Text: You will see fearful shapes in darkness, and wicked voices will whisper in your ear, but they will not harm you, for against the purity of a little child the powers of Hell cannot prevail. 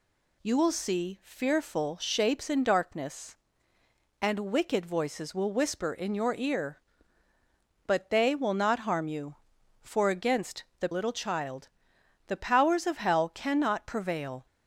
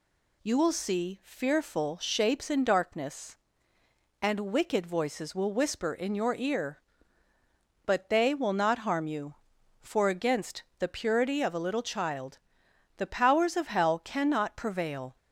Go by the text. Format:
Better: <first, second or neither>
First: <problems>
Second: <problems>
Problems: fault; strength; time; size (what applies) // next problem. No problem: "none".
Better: second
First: pauses between "against" and "the"; slight; at 10.6 s; 0.16 s long // skips "purity of a"; at 10.9 s // pauses between "child" and "the"; noticeable; at 11.6 s; 0.60 s long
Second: pauses between "against" and "the"; slight; at 10.6 s; 0.16 s long // pauses between "child" and "the"; noticeable; at 12.3 s; 0.60 s long